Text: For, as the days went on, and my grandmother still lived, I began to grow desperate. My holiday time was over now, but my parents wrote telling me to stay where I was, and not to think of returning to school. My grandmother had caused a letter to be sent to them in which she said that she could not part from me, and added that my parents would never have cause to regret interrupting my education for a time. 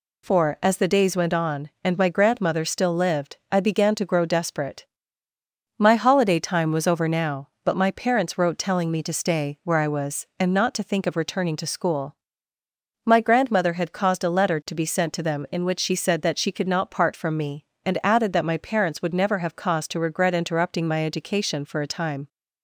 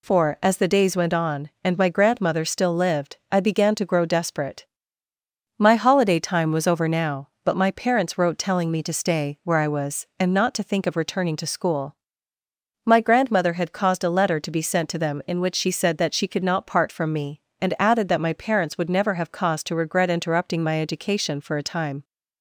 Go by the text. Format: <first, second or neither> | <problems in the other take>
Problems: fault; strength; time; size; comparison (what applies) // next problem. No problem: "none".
neither | none